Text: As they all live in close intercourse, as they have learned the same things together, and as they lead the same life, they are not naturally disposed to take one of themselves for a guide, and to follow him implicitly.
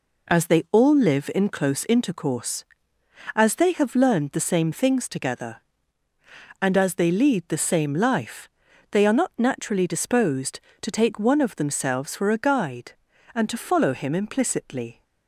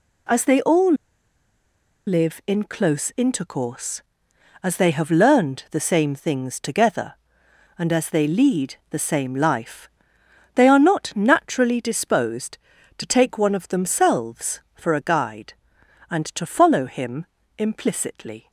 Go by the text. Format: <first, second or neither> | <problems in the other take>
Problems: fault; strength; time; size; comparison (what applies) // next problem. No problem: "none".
first | pauses between "all" and "live"; at 0.9 s; 1.1 s long // pauses between "lead" and "the"; slight; at 8.7 s; 0.16 s long // pauses between "him" and "implicitly"; slight; at 17.2 s; 0.32 s long